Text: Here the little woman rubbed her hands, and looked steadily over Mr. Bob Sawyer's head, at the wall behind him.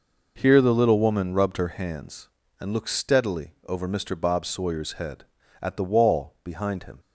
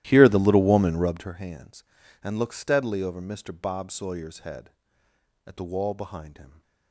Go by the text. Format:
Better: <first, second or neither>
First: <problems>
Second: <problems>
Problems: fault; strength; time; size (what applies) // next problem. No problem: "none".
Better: first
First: none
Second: starts louder than the rest; strong; until 1.3 s; 14 dB